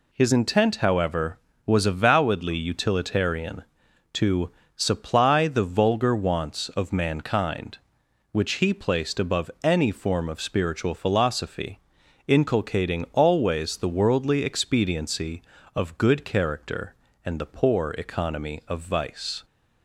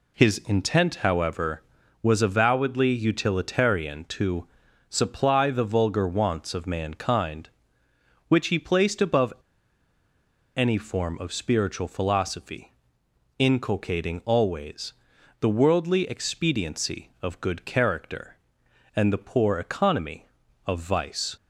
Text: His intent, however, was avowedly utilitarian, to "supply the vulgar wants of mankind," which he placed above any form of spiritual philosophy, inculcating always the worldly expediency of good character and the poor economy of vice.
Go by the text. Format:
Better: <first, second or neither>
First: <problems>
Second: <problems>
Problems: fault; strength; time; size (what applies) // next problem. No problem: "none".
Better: first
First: pauses between "to" and "supply"; slight; at 4.4 s; 0.26 s long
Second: pauses between "to" and "supply"; at 4.4 s; 0.42 s long // pauses between "above" and "any"; at 9.3 s; 1.2 s long // pauses between "always" and "the"; noticeable; at 14.9 s; 0.46 s long